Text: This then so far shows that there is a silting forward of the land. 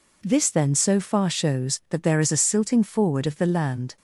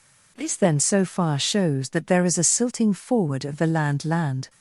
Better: first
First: none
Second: says "land" twice; at 4.0 s

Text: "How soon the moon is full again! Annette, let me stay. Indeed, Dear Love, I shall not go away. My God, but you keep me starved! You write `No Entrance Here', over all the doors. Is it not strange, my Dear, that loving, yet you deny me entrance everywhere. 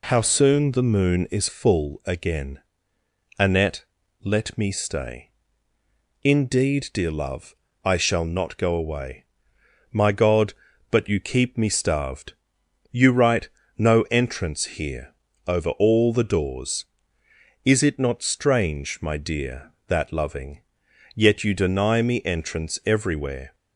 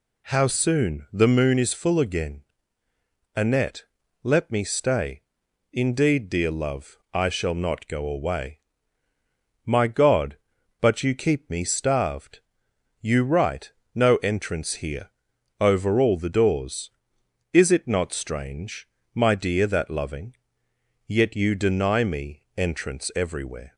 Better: neither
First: pauses between "write" and "No"; slight; at 13.4 s; 0.30 s long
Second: pauses between "write" and "No"; slight; at 13.7 s; 0.22 s long

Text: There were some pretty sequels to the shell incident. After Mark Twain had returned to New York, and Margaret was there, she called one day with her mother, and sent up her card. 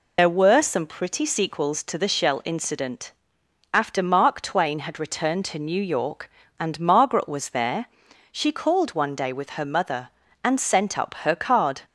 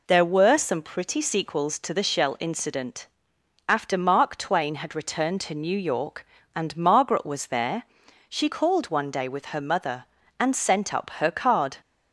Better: second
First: loses the start of "There"; at 0.1 s; 65 ms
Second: none

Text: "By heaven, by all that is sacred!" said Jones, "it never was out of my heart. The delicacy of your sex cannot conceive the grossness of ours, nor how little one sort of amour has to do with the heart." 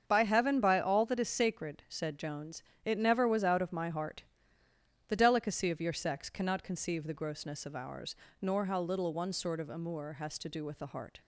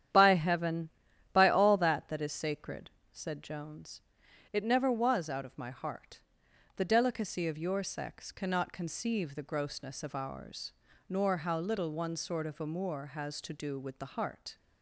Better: first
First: starts louder than the rest; until 1.0 s; 7 dB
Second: starts louder than the rest; strong; until 1.5 s; 10 dB // says "that" twice; at 2.0 s

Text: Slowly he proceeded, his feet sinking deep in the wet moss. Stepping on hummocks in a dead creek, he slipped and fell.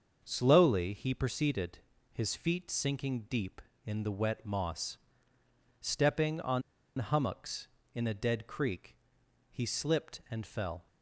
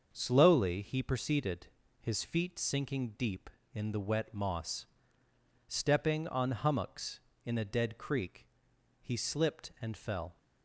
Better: second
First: starts louder than the rest; until 1.2 s; 6.5 dB // pauses between "on" and "hummocks"; at 6.6 s; 0.37 s long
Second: starts louder than the rest; until 1.1 s; 6.5 dB

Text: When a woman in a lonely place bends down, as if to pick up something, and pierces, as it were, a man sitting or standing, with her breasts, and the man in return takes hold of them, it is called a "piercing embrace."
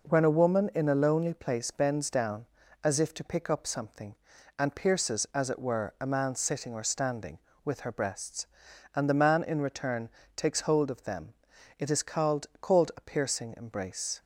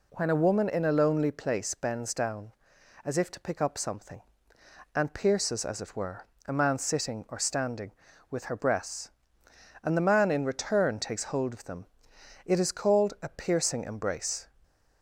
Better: second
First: pauses between "return" and "takes"; slight; at 10.0 s; 0.26 s long // says "called" twice; at 12.5 s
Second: none

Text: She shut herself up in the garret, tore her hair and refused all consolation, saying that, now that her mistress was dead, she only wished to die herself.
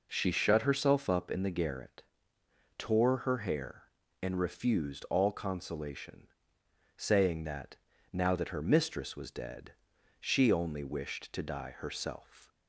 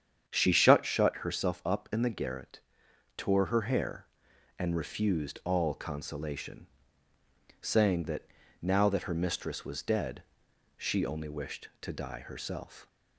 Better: first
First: none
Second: starts louder than the rest; strong; until 1.2 s; 8.5 dB // says "shut" twice; at 0.8 s

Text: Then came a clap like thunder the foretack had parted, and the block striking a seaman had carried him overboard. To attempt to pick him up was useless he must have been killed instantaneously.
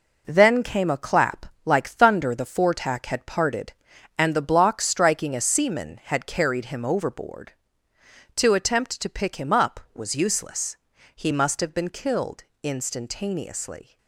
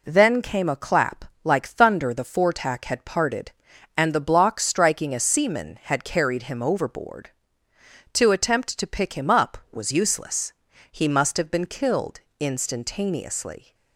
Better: second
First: gets quieter; throughout; 7 dB // pauses between "clap" and "like"; slight; at 1.4 s; 0.18 s long // pauses between "useless" and "he"; at 10.7 s; 0.42 s long // pauses between "killed" and "instantaneously"; slight; at 12.4 s; 0.18 s long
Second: pauses between "clap" and "like"; slight; at 1.2 s; 0.18 s long // pauses between "useless" and "he"; at 10.5 s; 0.42 s long // pauses between "killed" and "instantaneously"; slight; at 12.1 s; 0.18 s long

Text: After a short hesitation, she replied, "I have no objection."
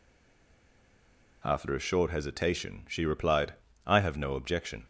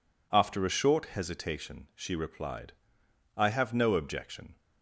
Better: second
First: stays silent before the first word; noticeable; until 1.4 s; 1.4 s long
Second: none

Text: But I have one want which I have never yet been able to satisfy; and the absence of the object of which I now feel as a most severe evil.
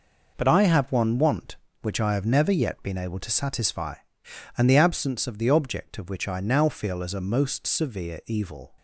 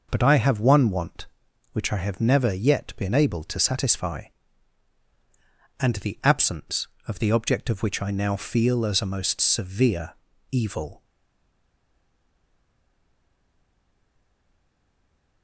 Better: first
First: none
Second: pauses between "severe" and "evil"; slight; at 10.1 s; 0.36 s long // stays silent after the last word; strong; from 11.0 s on; 4.4 s long

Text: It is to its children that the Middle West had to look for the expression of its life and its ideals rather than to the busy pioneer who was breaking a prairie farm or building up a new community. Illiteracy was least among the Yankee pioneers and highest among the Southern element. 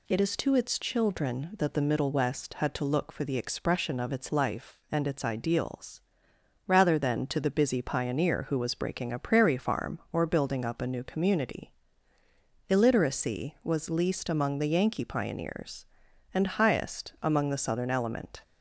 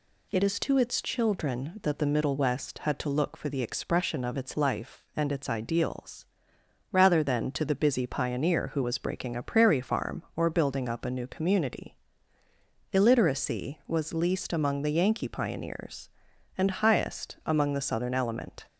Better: neither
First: pauses between "ideals" and "rather"; noticeable; at 5.9 s; 0.66 s long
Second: pauses between "ideals" and "rather"; noticeable; at 6.2 s; 0.66 s long

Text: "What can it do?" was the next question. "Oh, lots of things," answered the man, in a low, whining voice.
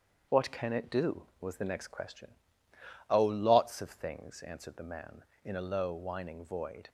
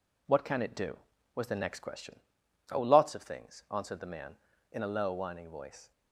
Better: second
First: starts louder than the rest; strong; until 1.4 s; 7.5 dB // says "void" for "voice"; at 6.4 s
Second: none

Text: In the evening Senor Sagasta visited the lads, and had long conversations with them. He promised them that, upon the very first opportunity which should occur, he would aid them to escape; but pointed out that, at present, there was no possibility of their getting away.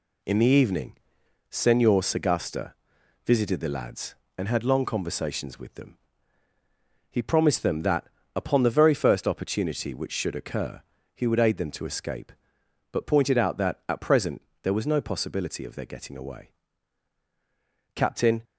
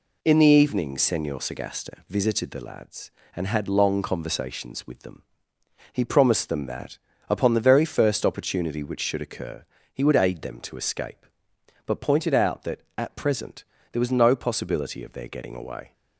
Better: second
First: pauses between "evening" and "Senor"; noticeable; at 0.9 s; 0.54 s long // pauses between "Sagasta" and "visited"; noticeable; at 2.7 s; 0.52 s long // goes on to say "Captain"; slight; from 17.9 s on; 0.48 s long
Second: none

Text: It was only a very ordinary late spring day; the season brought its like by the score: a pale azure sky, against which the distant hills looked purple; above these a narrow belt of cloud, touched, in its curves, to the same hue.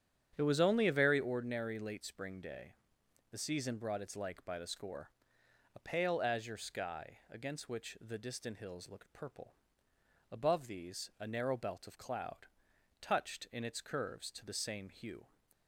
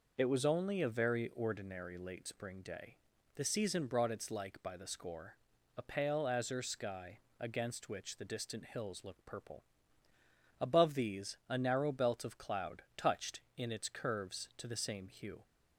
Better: second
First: starts louder than the rest; strong; until 1.2 s; 9 dB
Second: none

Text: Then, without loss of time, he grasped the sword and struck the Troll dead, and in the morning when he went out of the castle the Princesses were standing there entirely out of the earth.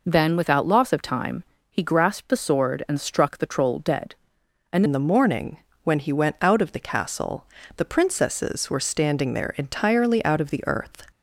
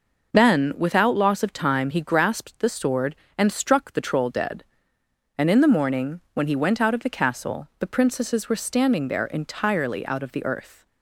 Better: second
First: changes voice at "in"; from 4.8 s on; 6.2 s long // pauses between "morning" and "when"; slight; at 5.5 s; 0.26 s long // pauses between "castle" and "the"; slight; at 7.4 s; 0.30 s long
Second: none

